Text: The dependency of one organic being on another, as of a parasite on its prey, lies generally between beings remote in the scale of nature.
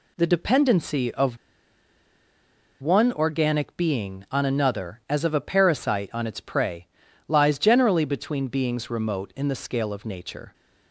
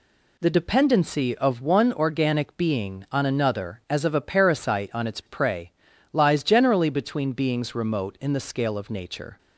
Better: second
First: pauses between "of" and "one"; strong; at 1.3 s; 1.4 s long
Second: none

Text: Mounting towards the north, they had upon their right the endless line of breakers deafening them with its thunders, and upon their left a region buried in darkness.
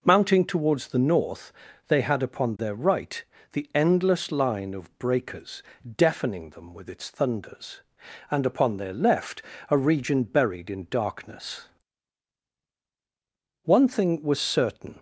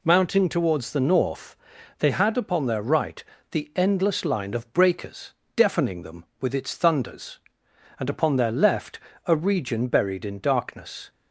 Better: second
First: pauses between "right" and "the"; slight; at 3.2 s; 0.28 s long // pauses between "breakers" and "deafening"; slight; at 5.6 s; 0.34 s long // pauses between "left" and "a"; slight; at 9.4 s; 0.28 s long // goes on to say "One thing was certain"; from 13.6 s on; 1.3 s long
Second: pauses between "right" and "the"; slight; at 3.2 s; 0.30 s long // pauses between "breakers" and "deafening"; slight; at 5.3 s; 0.22 s long // pauses between "left" and "a"; slight; at 8.9 s; 0.28 s long

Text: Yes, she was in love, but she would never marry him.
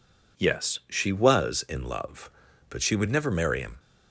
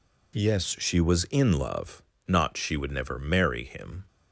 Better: first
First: none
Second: says "not" for "but"; at 2.2 s

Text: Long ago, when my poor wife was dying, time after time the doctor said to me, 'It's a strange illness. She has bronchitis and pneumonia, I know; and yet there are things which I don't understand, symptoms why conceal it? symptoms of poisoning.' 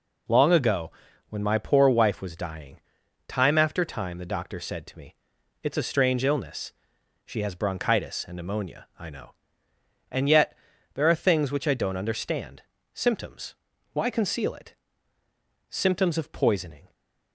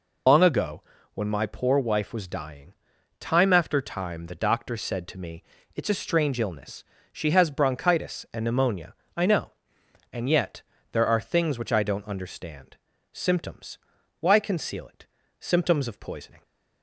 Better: first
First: pauses between "yet" and "there"; at 10.5 s; 0.40 s long // pauses between "symptoms" and "why"; at 13.5 s; 0.38 s long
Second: loses the start of "Long"; at 0.2 s; 130 ms // pauses between "yet" and "there"; slight; at 10.6 s; 0.30 s long // pauses between "symptoms" and "why"; at 13.7 s; 0.42 s long

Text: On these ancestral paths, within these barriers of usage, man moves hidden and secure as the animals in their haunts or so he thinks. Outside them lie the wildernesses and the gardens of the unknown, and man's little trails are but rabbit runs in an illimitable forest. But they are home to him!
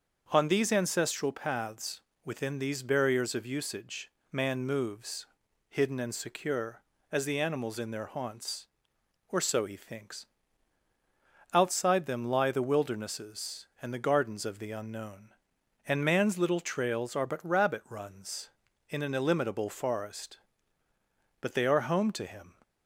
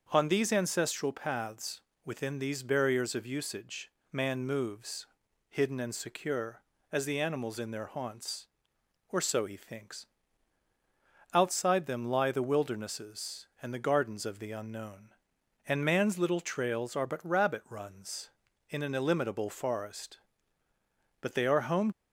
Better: first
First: starts louder than the rest; until 1.3 s; 6.5 dB // pauses between "moves" and "hidden"; at 5.2 s; 0.44 s long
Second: starts louder than the rest; until 1.1 s; 6.5 dB // pauses between "moves" and "hidden"; at 5.0 s; 0.44 s long // stops before "to him"; at 21.9 s

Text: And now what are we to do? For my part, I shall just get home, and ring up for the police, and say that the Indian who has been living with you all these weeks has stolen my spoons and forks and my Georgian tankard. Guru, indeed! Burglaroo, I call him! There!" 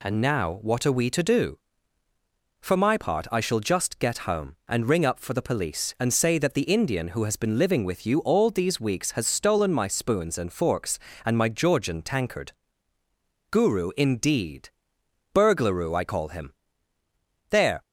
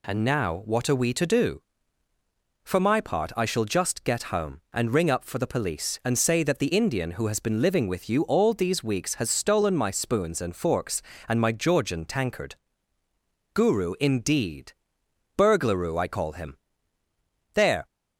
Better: neither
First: none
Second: none

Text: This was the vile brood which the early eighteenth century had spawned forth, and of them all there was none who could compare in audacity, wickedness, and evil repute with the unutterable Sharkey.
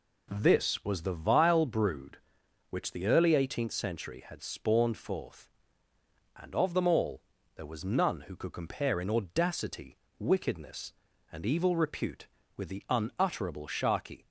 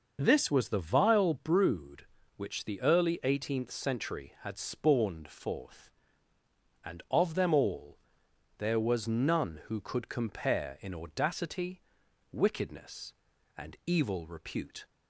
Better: first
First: pauses between "all" and "there"; slight; at 7.2 s; 0.32 s long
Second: starts louder than the rest; noticeable; until 1.2 s; 6 dB // pauses between "all" and "there"; noticeable; at 7.9 s; 0.62 s long // stops before "with the unutterable Sharkey"; at 14.8 s

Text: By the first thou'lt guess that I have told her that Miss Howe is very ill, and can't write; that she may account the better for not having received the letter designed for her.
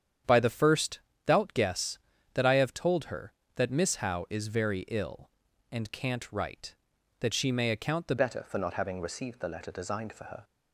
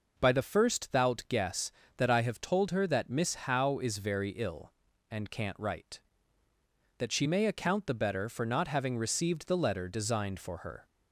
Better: second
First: starts louder than the rest; strong; until 1.5 s; 8.5 dB // pauses between "first" and "thou'lt"; slight; at 0.9 s; 0.26 s long // changes voice at "better"; from 8.1 s on; 2.3 s long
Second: none

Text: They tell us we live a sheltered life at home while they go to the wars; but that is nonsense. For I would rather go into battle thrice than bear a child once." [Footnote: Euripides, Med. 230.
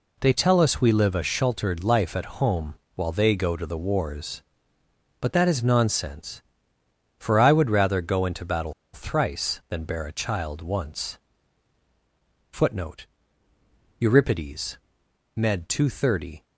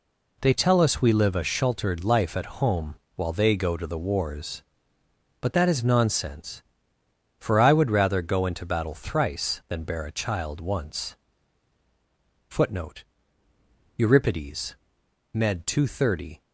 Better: second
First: pauses between "home" and "while"; slight; at 2.7 s; 0.22 s long // pauses between "battle" and "thrice"; slight; at 8.7 s; 0.20 s long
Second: pauses between "home" and "while"; slight; at 2.9 s; 0.22 s long

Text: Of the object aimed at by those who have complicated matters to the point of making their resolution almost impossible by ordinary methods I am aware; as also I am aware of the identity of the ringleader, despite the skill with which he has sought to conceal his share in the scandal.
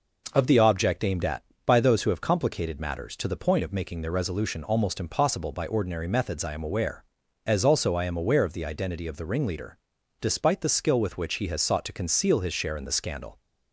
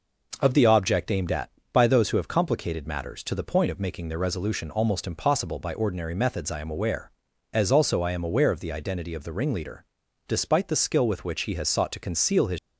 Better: first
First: none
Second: stops before "share in the scandal"; at 12.5 s

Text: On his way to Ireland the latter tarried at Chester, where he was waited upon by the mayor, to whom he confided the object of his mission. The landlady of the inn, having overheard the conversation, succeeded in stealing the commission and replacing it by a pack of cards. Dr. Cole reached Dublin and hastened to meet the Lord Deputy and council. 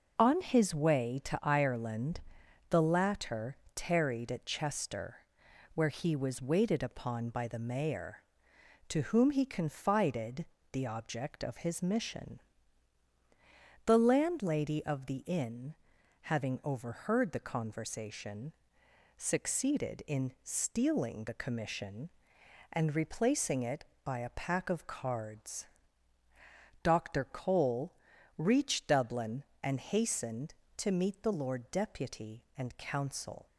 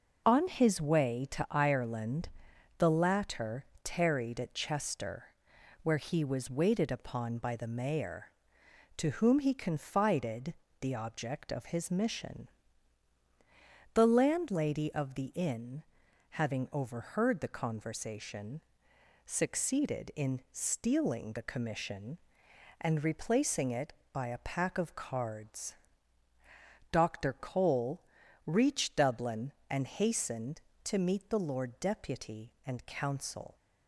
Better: neither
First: pauses between "Ireland" and "the"; noticeable; at 2.2 s; 0.48 s long // pauses between "latter" and "tarried"; slight; at 3.5 s; 0.18 s long // pauses between "confided" and "the"; slight; at 10.4 s; 0.26 s long // pauses between "Cole" and "reached"; at 27.9 s; 0.42 s long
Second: pauses between "Ireland" and "the"; noticeable; at 2.2 s; 0.48 s long // pauses between "latter" and "tarried"; slight; at 3.6 s; 0.18 s long // pauses between "confided" and "the"; slight; at 10.5 s; 0.26 s long // pauses between "Cole" and "reached"; at 28.0 s; 0.42 s long

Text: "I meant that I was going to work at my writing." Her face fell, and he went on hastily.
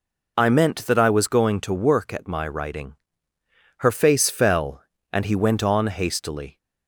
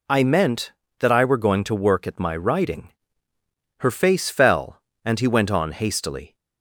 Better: first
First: none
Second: says "were" for "was"; at 1.2 s

